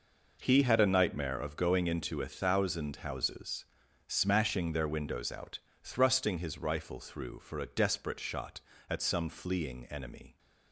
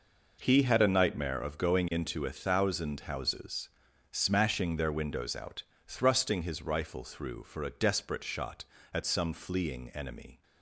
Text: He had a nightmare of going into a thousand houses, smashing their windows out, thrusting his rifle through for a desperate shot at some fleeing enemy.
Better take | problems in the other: neither | none

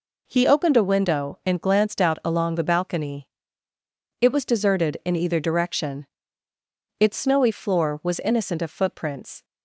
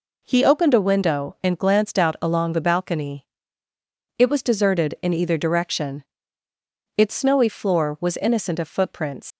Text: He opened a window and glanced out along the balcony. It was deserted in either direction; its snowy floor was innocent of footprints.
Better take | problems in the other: first | leaves "footprints" unfinished; at 9.3 s; 115 ms

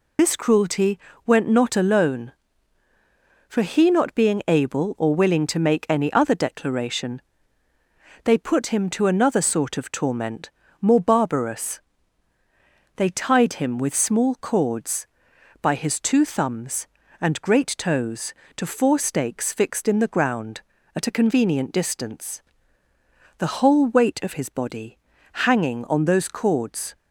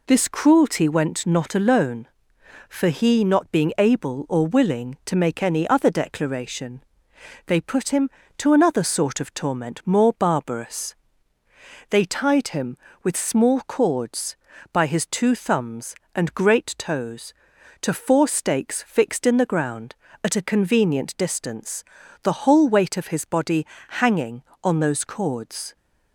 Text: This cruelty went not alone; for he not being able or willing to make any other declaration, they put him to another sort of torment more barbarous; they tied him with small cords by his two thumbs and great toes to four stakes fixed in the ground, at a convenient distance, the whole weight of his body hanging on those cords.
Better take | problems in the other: second | loses the start of "This"; at 0.1 s; 45 ms // pauses between "cruelty" and "went"; slight; at 0.9 s; 0.26 s long // pauses between "torment" and "more"; slight; at 10.5 s; 0.32 s long // pauses between "body" and "hanging"; noticeable; at 24.9 s; 0.50 s long; slight in the second

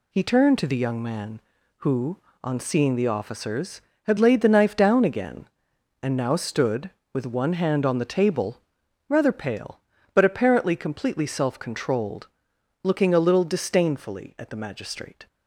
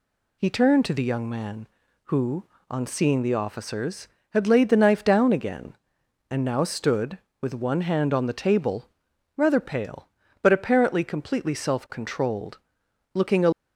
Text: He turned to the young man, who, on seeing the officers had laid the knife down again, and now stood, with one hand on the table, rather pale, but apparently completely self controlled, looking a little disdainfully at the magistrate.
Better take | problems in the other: first | stops before "little disdainfully at the magistrate"; at 13.5 s

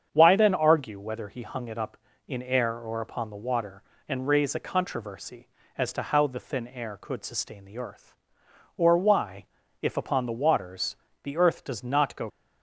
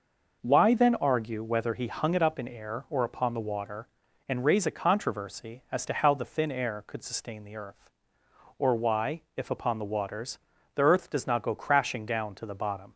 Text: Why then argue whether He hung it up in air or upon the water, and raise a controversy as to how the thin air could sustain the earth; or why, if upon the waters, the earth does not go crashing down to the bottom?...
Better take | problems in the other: second | starts louder than the rest; strong; until 1.1 s; 7.5 dB // stops before "crashing down to the bottom"; at 12.2 s

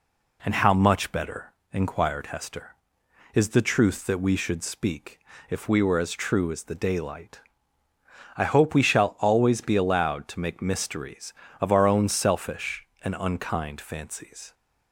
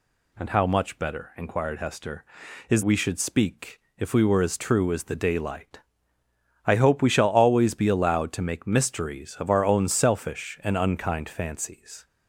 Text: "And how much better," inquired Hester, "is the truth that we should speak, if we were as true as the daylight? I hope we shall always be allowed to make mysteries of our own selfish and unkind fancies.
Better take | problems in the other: first | skips "the truth that"; at 2.8 s

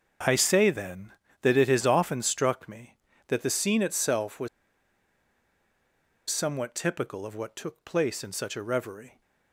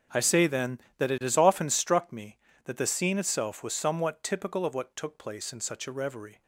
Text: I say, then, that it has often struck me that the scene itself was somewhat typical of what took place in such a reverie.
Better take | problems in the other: second | starts louder than the rest; until 1.5 s; 7 dB; also in the second // pauses between "was" and "somewhat"; strong; at 4.4 s; 1.8 s long

